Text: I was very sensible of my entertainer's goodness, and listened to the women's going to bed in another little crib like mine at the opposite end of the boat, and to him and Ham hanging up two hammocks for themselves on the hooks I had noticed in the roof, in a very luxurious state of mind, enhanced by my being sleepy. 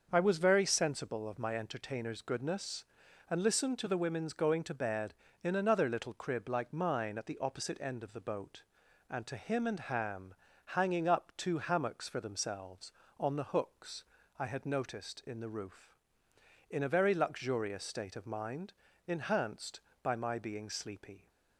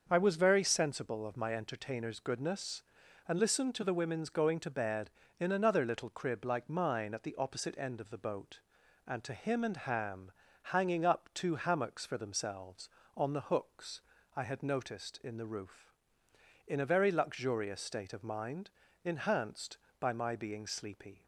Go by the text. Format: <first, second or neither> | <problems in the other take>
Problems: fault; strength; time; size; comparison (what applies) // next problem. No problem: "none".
neither | starts louder than the rest; the same in both // pauses between "Ham" and "hanging"; the same in both // pauses between "hooks" and "I"; slight; the same in both